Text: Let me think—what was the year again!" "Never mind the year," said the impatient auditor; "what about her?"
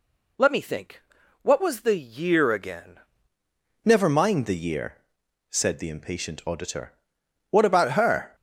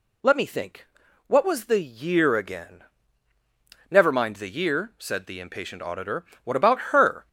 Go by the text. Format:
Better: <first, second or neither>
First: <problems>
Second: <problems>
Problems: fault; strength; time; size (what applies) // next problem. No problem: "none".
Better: second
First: changes voice at "Never"; from 3.8 s on; 4.5 s long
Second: none